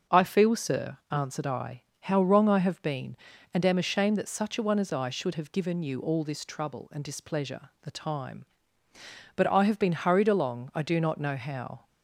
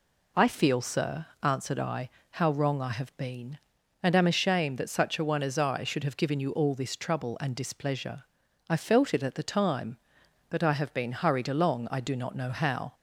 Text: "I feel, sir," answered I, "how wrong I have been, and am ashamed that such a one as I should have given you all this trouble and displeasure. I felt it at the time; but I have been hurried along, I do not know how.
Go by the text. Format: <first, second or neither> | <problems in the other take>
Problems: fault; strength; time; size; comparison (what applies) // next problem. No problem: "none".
second | starts louder than the rest; until 1.2 s; 6.5 dB // skips "I felt it at"; at 7.7 s